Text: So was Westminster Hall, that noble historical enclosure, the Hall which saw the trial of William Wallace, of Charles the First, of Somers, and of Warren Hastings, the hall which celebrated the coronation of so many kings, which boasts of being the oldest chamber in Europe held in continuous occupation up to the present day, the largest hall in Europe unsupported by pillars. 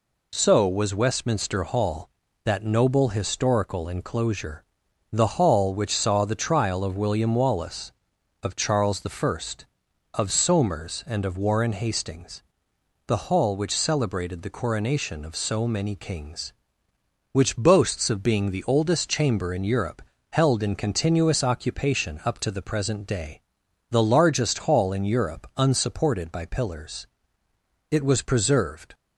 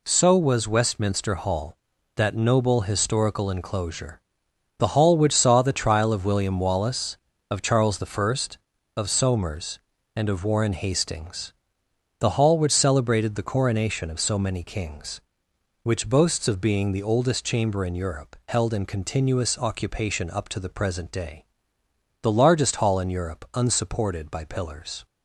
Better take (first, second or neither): second